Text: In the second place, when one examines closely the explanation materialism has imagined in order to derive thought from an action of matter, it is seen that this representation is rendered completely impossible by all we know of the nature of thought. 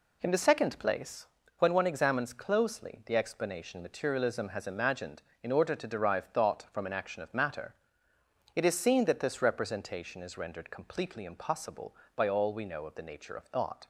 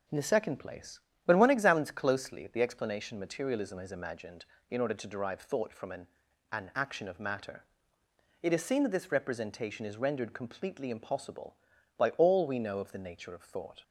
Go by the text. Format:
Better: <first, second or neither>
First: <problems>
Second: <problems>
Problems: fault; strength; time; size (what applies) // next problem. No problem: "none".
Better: first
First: none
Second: says "an" twice; at 6.5 s